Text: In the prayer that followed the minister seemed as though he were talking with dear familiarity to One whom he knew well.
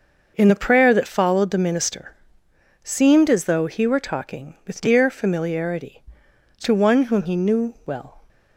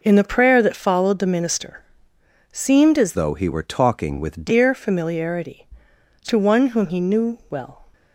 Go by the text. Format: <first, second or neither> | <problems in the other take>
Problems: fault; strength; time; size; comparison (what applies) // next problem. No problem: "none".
first | pauses between "minister" and "seemed"; noticeable; at 1.8 s; 0.68 s long; noticeable in the first // changes voice from "though" to "with"; from 3.1 to 4.4 s; 1.3 s long